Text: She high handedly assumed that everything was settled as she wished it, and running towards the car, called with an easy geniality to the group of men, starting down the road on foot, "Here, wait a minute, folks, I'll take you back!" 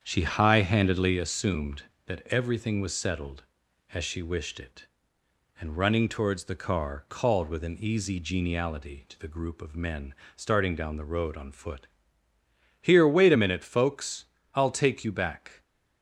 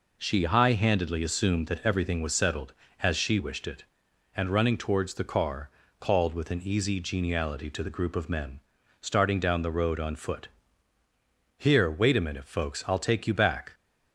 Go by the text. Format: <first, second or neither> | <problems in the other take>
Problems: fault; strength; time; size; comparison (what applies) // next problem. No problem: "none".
second | starts louder than the rest; strong; until 1.3 s; 7.5 dB